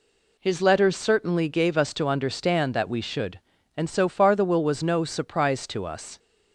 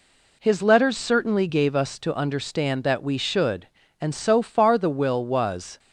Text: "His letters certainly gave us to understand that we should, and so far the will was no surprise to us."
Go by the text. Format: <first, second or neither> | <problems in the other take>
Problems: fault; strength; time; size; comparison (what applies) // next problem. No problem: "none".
first | stops before "no surprise to us"; at 5.7 s